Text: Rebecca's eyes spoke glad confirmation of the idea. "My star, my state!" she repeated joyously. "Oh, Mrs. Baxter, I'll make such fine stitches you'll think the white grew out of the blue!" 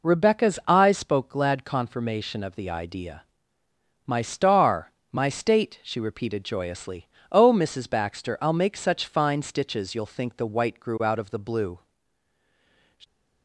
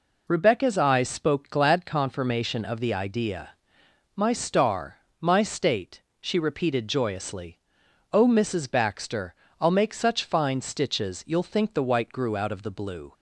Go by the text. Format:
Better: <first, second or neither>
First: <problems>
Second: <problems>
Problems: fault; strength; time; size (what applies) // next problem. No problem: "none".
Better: neither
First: none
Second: none